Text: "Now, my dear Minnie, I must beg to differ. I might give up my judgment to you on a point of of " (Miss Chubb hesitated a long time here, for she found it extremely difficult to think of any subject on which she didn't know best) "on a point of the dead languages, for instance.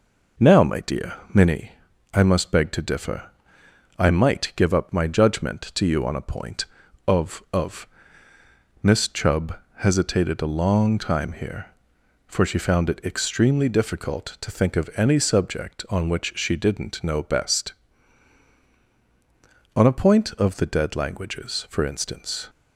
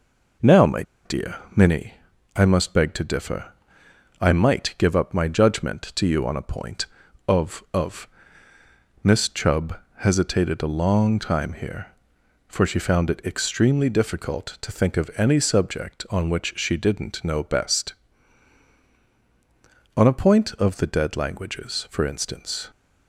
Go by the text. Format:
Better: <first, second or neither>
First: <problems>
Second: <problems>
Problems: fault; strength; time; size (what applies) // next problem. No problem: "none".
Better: first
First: pauses between "dear" and "Minnie"; slight; at 1.1 s; 0.18 s long // pauses between "Chubb" and "hesitated"; slight; at 9.5 s; 0.22 s long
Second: pauses between "my" and "dear"; slight; at 0.8 s; 0.22 s long // pauses between "dear" and "Minnie"; slight; at 1.3 s; 0.18 s long // pauses between "Chubb" and "hesitated"; slight; at 9.7 s; 0.22 s long